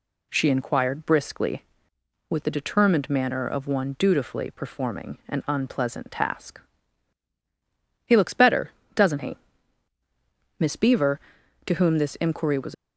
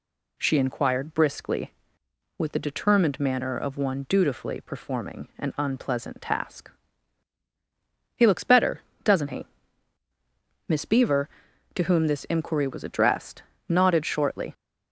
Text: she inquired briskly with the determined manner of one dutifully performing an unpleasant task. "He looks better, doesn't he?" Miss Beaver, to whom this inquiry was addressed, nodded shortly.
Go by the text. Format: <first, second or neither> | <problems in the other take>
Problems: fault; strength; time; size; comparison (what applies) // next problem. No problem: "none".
second | stops before "addressed nodded shortly"; at 12.7 s